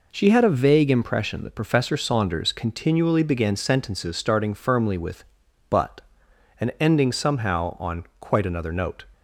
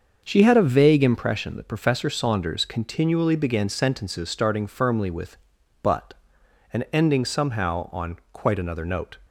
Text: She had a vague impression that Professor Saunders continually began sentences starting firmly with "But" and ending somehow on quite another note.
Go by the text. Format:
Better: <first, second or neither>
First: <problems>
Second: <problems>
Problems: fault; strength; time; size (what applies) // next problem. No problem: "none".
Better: first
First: none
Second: starts louder than the rest; until 1.4 s; 6.5 dB